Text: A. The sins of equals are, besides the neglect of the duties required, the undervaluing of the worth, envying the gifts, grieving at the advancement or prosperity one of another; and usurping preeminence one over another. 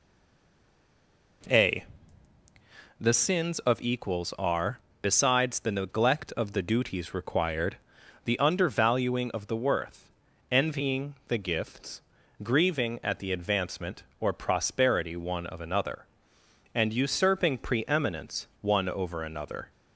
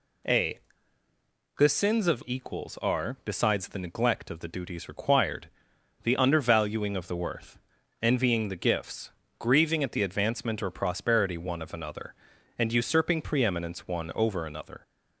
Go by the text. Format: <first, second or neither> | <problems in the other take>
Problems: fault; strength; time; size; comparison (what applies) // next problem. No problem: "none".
second | stays silent before the first word; noticeable; until 1.4 s; 1.4 s long